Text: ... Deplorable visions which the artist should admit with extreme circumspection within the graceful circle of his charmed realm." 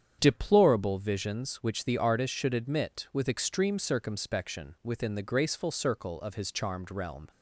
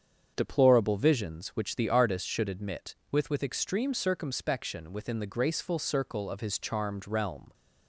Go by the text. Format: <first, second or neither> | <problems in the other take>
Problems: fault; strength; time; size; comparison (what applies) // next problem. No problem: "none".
first | starts louder than the rest; strong; until 1.3 s; 7.5 dB; strong in the first // says "with" twice; at 3.2 s